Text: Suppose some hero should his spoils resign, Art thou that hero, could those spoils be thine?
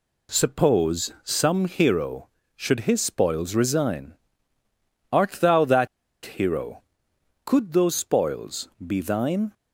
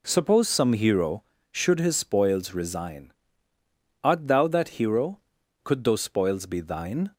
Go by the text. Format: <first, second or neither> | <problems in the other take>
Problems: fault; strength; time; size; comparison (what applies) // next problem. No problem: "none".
second | pauses between "that" and "hero"; at 5.8 s; 0.37 s long // pauses between "spoils" and "be"; slight; at 8.6 s; 0.16 s long